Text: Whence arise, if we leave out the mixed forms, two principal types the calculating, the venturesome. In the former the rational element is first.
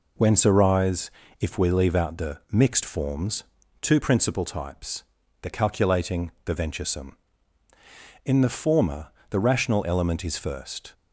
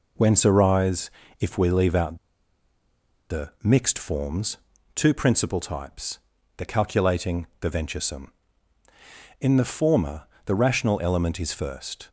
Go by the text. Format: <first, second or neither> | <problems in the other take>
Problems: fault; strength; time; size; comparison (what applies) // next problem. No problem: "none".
first | pauses between "out" and "the"; at 2.1 s; 1.1 s long // pauses between "types" and "the"; at 6.1 s; 0.38 s long; also in the first // pauses between "former" and "the"; slight; at 10.2 s; 0.20 s long; slight in the first